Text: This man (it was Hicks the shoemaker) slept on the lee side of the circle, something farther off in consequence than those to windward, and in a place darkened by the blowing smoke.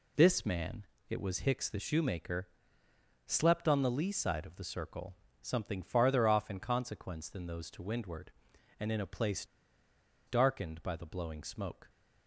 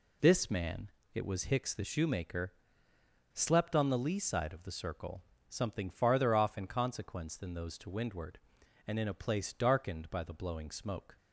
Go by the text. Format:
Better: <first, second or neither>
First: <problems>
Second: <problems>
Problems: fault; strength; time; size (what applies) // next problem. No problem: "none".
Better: second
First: pauses between "place" and "darkened"; noticeable; at 9.4 s; 0.81 s long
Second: none